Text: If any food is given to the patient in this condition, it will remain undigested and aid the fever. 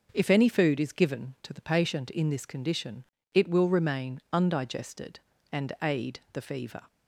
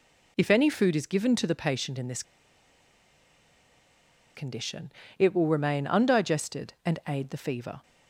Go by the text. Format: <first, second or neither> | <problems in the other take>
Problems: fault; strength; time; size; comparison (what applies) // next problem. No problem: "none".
first | pauses between "this" and "condition"; strong; at 2.2 s; 2.1 s long